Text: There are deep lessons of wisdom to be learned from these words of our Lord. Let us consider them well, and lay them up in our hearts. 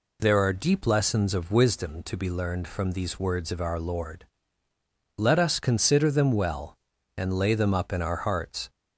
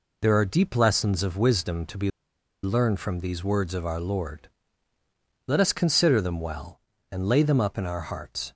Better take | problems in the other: first | pauses between "be" and "learned"; noticeable; at 2.0 s; 0.53 s long

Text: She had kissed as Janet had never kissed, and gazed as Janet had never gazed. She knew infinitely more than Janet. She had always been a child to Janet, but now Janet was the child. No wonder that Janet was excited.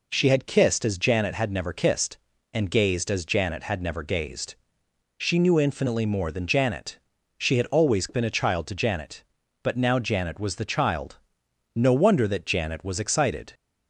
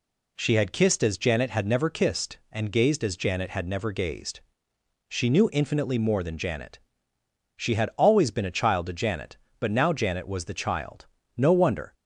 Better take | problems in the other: first | stops before "that Janet was excited"; at 11.9 s

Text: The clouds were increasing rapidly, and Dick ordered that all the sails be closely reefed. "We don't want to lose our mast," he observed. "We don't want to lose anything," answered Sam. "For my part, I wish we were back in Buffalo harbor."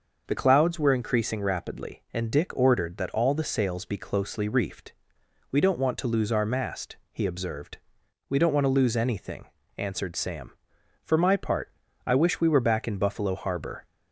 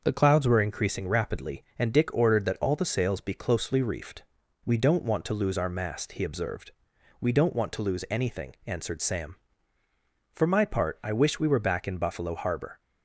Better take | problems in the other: neither | starts louder than the rest; the same in both

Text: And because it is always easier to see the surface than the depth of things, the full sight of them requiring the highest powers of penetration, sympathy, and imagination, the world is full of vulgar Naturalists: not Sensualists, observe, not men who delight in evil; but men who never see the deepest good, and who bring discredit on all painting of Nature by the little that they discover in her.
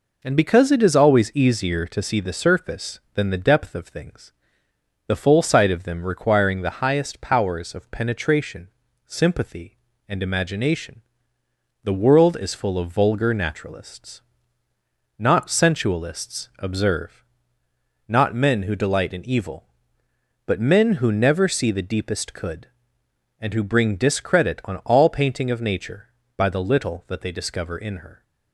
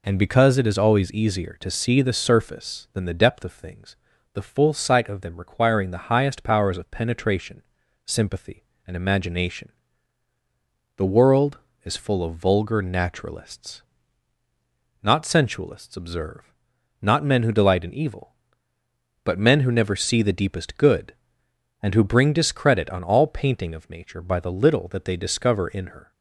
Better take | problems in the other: second | says "could" for "good"; at 22.3 s

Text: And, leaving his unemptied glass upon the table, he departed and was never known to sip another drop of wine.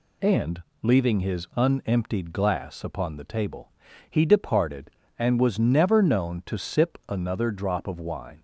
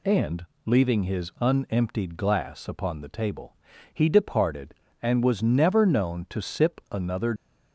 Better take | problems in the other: first | stops before "drop of wine"; at 7.3 s

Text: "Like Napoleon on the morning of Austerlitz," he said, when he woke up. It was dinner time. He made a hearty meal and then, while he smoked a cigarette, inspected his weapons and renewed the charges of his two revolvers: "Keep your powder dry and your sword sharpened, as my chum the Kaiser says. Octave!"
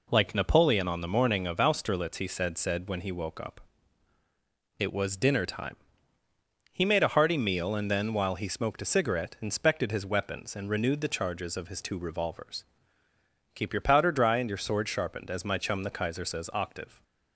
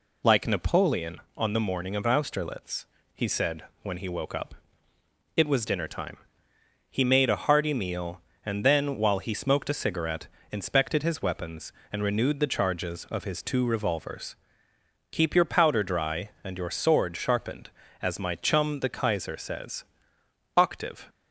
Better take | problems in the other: second | says "said" twice; at 2.5 s

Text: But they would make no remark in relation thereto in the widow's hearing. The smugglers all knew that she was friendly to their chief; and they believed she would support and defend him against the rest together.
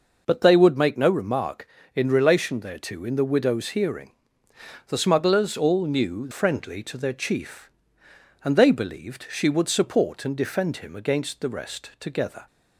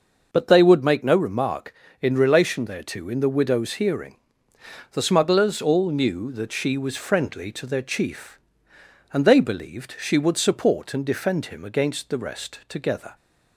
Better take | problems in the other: second | skips "that she was"; at 6.2 s

